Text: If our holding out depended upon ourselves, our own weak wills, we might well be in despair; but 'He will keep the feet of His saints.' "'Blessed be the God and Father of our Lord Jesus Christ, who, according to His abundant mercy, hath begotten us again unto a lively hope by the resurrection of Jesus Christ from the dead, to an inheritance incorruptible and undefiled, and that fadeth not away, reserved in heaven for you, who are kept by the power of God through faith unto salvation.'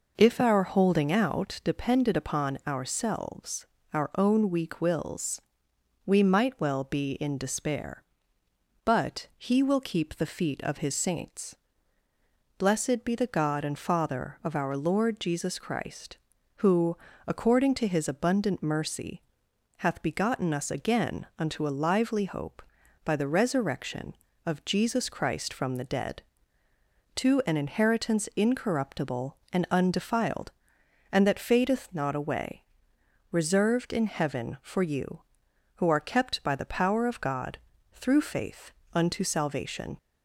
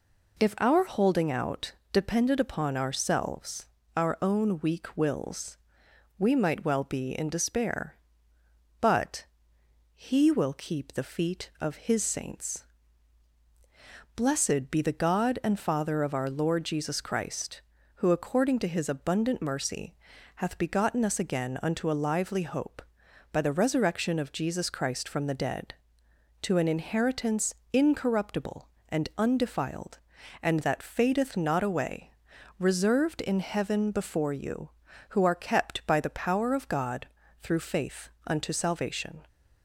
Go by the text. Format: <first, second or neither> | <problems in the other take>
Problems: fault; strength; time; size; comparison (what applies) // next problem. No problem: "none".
first | pauses between "out" and "depended"; slight; at 1.7 s; 0.20 s long // pauses between "but" and "He"; noticeable; at 9.2 s; 0.70 s long // pauses between "inheritance" and "incorruptible"; slight; at 27.5 s; 0.18 s long // says "before" for "for"; at 33.9 s // pauses between "God" and "through"; slight; at 37.0 s; 0.34 s long; slight in the first // pauses between "faith" and "unto"; slight; at 38.0 s; 0.16 s long; slight in the first